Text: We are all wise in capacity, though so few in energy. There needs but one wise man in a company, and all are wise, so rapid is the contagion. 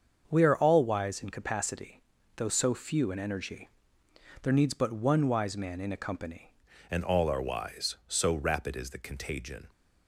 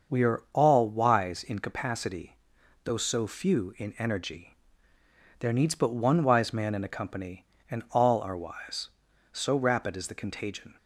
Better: second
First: starts louder than the rest; until 1.2 s; 7 dB // changes voice at "and"; from 6.9 s on; 2.7 s long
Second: starts louder than the rest; until 1.2 s; 6.5 dB

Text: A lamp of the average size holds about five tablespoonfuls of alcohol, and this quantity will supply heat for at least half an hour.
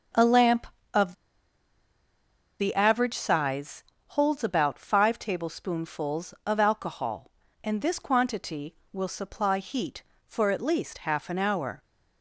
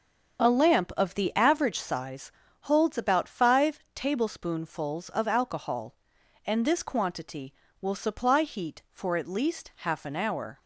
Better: second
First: starts louder than the rest; until 2.8 s; 7 dB // pauses between "of" and "the"; strong; at 1.1 s; 1.4 s long // pauses between "size" and "holds"; slight; at 3.8 s; 0.26 s long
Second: starts louder than the rest; until 1.5 s; 7 dB // pauses between "size" and "holds"; slight; at 2.3 s; 0.30 s long

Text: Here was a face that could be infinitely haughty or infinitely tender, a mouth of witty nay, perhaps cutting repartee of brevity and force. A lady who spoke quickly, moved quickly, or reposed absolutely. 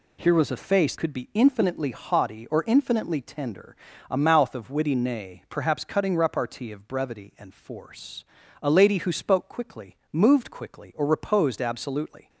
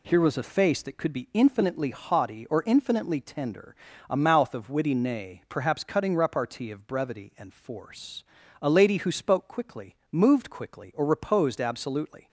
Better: second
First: skips "that"; at 0.9 s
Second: none

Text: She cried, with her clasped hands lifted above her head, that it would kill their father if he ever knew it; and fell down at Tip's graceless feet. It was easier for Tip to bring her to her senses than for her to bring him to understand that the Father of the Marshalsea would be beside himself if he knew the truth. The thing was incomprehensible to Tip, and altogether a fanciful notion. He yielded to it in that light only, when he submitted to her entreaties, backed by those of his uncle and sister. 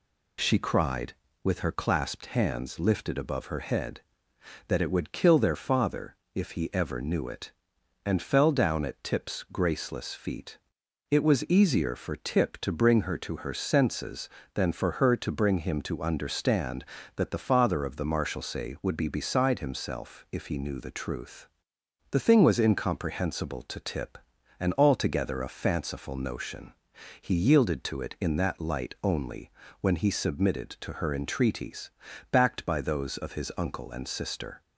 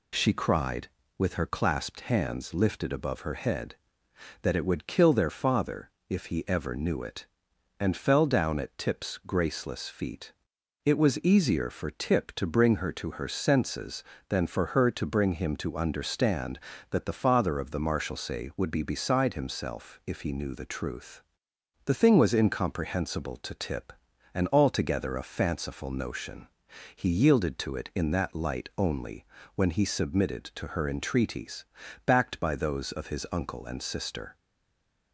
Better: first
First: pauses between "father" and "if"; slight; at 6.1 s; 0.18 s long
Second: pauses between "father" and "if"; slight; at 5.8 s; 0.18 s long // stays silent after the last word; slight; from 34.3 s on; 0.8 s long

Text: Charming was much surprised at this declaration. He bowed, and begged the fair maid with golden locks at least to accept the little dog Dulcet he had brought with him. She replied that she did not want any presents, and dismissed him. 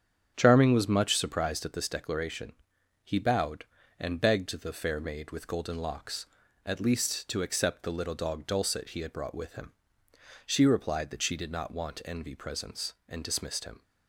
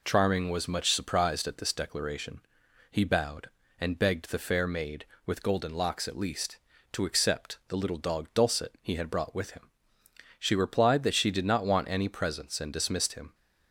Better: second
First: starts louder than the rest; strong; until 1.3 s; 8 dB // says "envy" for "any"; at 12.0 s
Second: none

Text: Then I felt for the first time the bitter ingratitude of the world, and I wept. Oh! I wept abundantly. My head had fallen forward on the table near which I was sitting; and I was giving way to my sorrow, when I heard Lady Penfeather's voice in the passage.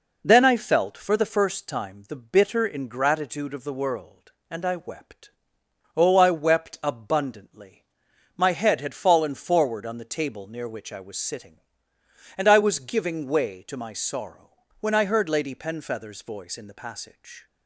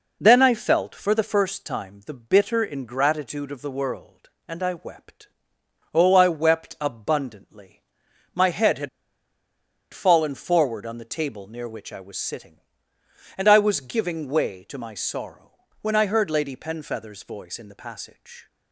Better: first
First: none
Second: pauses between "had" and "fallen"; at 8.8 s; 1.0 s long

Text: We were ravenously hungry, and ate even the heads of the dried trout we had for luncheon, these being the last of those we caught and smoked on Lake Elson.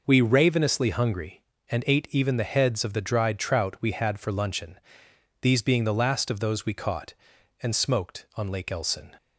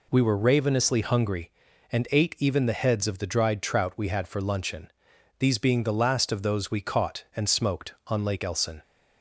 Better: second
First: skips "were"; at 0.2 s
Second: none

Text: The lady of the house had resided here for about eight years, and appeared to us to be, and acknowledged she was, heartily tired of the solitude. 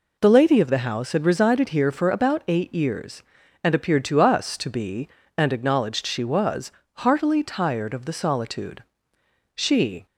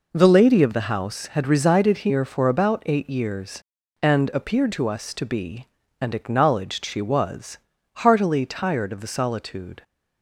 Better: second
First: goes on to say "She"; from 9.5 s on; 0.50 s long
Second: none

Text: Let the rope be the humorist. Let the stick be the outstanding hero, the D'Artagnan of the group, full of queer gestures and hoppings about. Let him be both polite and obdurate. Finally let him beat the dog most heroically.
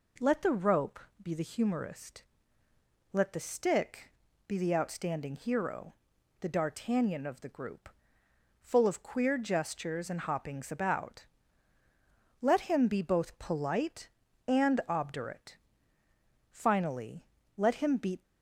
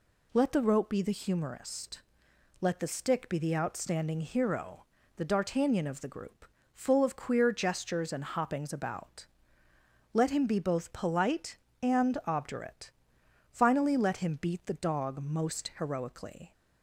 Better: second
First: pauses between "rope" and "be"; slight; at 0.9 s; 0.22 s long // pauses between "stick" and "be"; at 4.0 s; 0.38 s long // pauses between "Finally" and "let"; slight; at 17.2 s; 0.36 s long // stops before "the dog most heroically"; at 18.2 s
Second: none

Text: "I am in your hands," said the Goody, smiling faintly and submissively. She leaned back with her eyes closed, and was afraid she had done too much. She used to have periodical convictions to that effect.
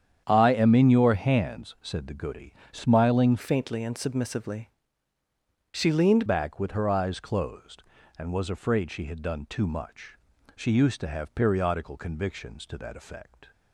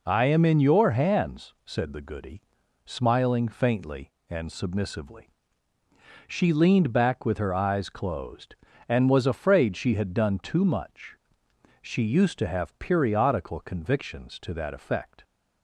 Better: second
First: starts louder than the rest; strong; until 1.2 s; 8.5 dB // changes voice from "faintly" to "leaned"; from 3.3 to 6.2 s; 2.9 s long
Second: none

